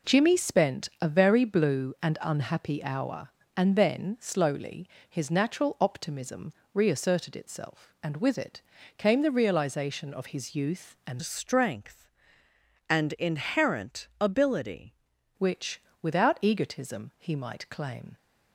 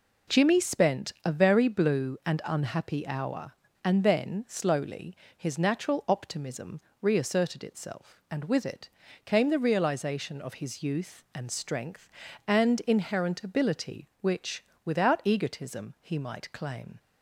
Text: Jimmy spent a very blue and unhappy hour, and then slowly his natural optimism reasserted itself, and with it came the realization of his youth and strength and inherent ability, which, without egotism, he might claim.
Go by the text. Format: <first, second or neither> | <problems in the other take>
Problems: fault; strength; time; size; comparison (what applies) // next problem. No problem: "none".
second | pauses between "slowly" and "his"; slight; at 4.8 s; 0.22 s long; slight in the second // pauses between "optimism" and "reasserted"; slight; at 6.5 s; 0.22 s long; slight in the second // pauses between "it" and "came"; at 8.6 s; 0.38 s long; also in the second // changes voice from "strength" to "ability"; from 11.2 to 14.9 s; 3.7 s long